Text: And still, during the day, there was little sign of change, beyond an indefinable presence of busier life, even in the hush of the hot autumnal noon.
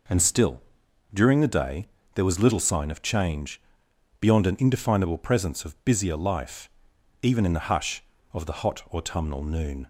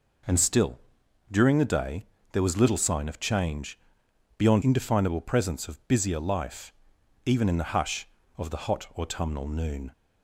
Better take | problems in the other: first | skips "an"; at 4.6 s

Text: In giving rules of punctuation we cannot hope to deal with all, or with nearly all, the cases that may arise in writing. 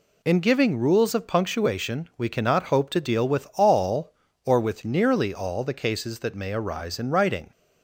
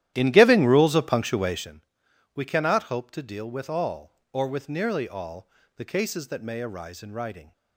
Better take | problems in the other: first | starts louder than the rest; strong; until 1.8 s; 12.5 dB // pauses between "punctuation" and "we"; noticeable; at 1.8 s; 0.52 s long

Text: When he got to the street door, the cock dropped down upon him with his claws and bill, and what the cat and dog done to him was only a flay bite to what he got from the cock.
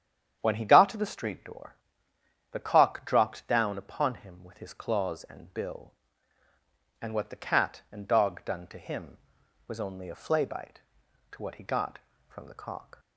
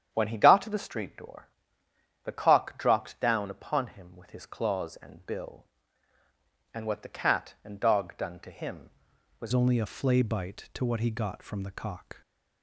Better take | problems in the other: first | starts louder than the rest; strong; until 1.1 s; 9 dB; strong in the first // changes voice at "only"; from 9.5 s on; 2.7 s long

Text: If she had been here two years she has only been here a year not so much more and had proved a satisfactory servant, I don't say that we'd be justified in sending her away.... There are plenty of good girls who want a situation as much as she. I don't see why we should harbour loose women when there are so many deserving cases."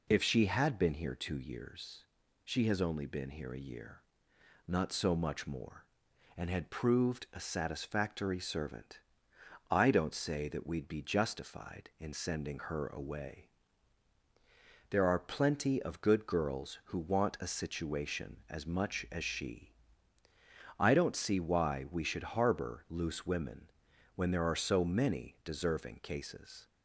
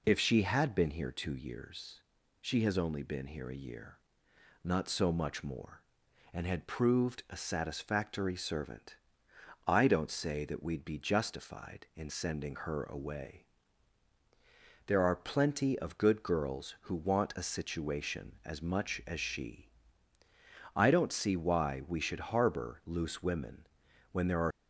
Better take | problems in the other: first | pauses between "years" and "she"; at 1.9 s; 0.40 s long; also in the first // pauses between "year" and "not"; noticeable; at 3.9 s; 0.66 s long; noticeable in the first // pauses between "women" and "when"; noticeable; at 23.6 s; 0.46 s long; noticeable in the first // stops before "so many deserving cases"; at 24.5 s

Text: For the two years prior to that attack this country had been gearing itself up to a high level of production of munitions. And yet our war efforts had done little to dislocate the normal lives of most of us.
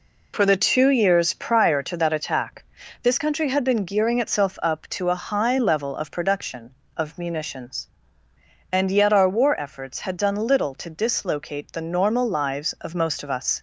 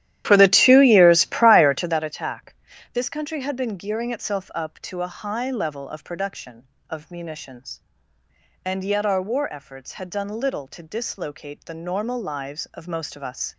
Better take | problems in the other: first | starts louder than the rest; strong; until 2.1 s; 12.5 dB // pauses between "attack" and "this"; at 2.5 s; 0.38 s long; also in the first

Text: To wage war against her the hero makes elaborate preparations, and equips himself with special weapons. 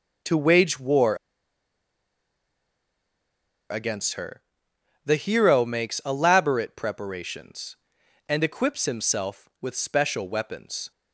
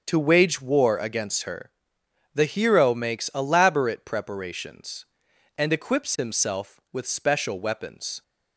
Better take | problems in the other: second | starts louder than the rest; until 3.7 s; 7 dB; also in the second // pauses between "war" and "against"; strong; at 1.1 s; 2.5 s long // pauses between "her" and "the"; noticeable; at 4.4 s; 0.64 s long; noticeable in the second

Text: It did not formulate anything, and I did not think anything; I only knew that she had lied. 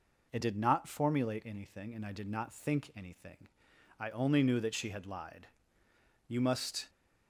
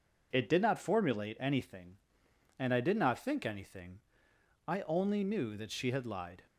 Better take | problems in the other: second | goes on to say "You must"; noticeable; from 6.2 s on; 0.62 s long

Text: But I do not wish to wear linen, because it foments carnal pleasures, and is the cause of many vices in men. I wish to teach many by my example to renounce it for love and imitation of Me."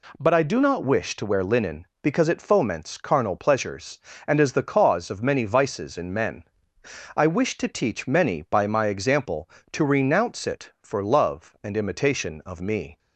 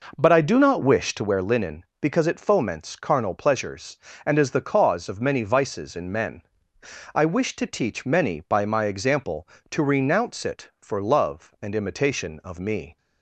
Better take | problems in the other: first | starts louder than the rest; noticeable; until 1.4 s; 5 dB

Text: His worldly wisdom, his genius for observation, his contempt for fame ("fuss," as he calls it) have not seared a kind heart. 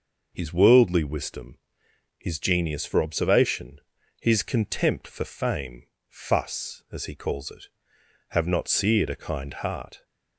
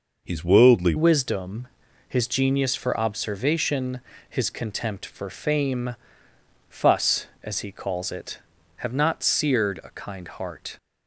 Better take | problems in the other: first | changes voice at "wisdom"; from 0.9 s on; 9.8 s long

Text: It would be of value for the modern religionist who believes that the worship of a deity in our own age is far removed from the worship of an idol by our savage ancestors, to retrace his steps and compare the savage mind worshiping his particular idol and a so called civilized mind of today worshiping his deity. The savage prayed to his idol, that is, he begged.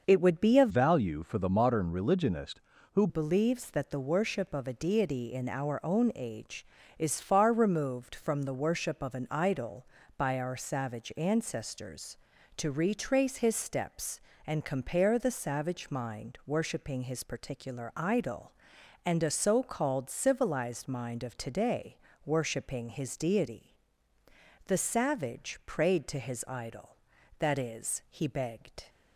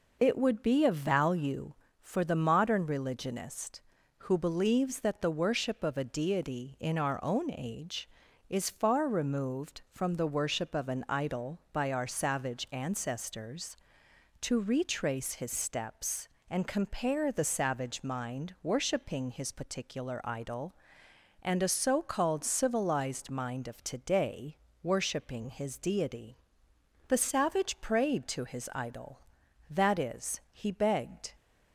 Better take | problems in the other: second | starts louder than the rest; until 1.0 s; 6 dB // changes voice from "value" to "who"; from 0.6 to 3.0 s; 2.4 s long // pauses between "today" and "worshiping"; slight; at 21.9 s; 0.28 s long; slight in the second

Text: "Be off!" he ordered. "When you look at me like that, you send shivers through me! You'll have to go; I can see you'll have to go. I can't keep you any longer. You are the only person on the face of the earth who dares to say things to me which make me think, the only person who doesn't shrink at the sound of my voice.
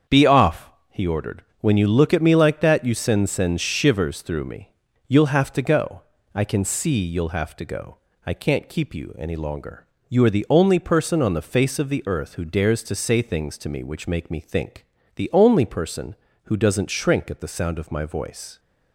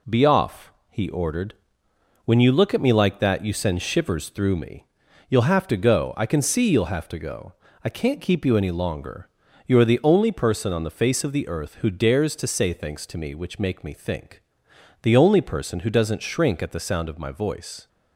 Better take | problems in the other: second | starts louder than the rest; strong; until 1.2 s; 7.5 dB // says "send" twice; at 3.2 s

